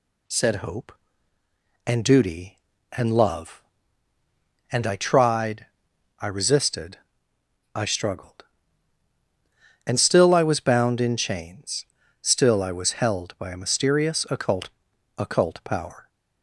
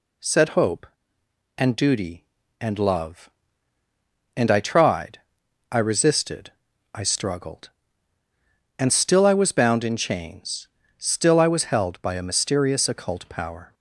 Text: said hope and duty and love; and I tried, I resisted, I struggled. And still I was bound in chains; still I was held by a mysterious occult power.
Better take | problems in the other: second | says "occult" twice; at 15.1 s

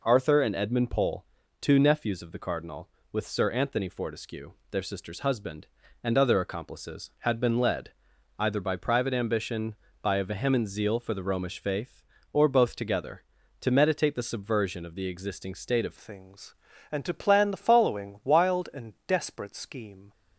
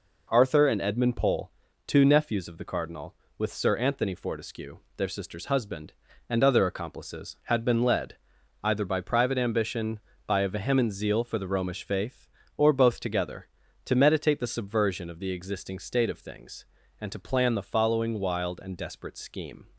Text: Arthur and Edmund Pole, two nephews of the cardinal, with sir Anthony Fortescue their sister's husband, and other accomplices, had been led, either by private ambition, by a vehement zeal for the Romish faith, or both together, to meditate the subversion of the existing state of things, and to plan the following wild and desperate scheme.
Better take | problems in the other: second | pauses between "Fortescue" and "their"; slight; at 4.5 s; 0.20 s long; slight in the second // changes voice at "things"; from 15.9 s on; 4.2 s long

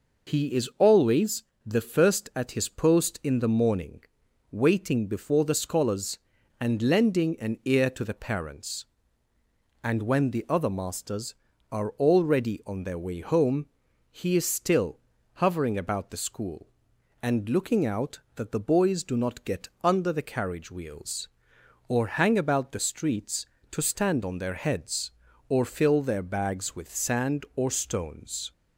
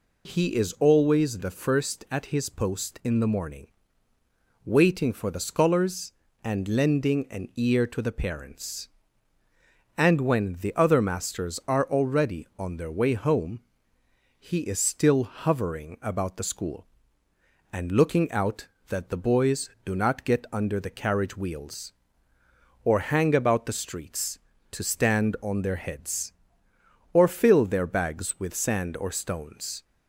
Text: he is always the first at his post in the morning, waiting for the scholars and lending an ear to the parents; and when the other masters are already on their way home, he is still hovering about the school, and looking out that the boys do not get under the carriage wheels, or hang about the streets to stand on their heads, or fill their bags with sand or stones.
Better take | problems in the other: second | pauses between "always" and "the"; slight; at 1.4 s; 0.24 s long // says "before" for "for"; at 5.0 s // pauses between "still" and "hovering"; slight; at 14.9 s; 0.36 s long

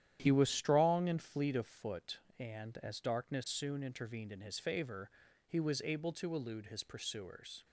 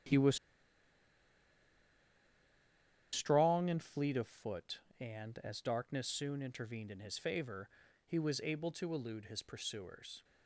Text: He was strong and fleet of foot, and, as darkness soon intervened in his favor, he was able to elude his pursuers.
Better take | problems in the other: first | starts louder than the rest; strong; until 3.8 s; 11 dB; strong in the first // pauses between "was" and "strong"; strong; at 0.3 s; 2.7 s long

